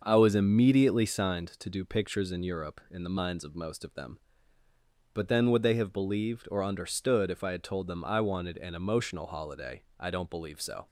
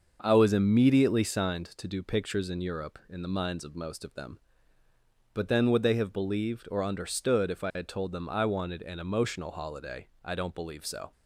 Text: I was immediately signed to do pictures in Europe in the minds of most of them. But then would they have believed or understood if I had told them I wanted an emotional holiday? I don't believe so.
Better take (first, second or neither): neither